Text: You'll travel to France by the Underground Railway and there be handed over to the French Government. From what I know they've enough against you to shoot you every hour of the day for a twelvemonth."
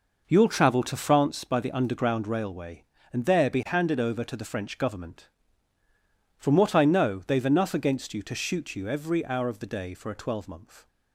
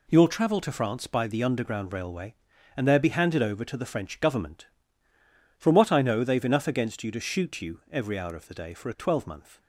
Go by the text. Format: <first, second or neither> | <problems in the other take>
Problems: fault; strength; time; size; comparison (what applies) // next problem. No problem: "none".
second | starts louder than the rest; noticeable; until 1.4 s; 5.5 dB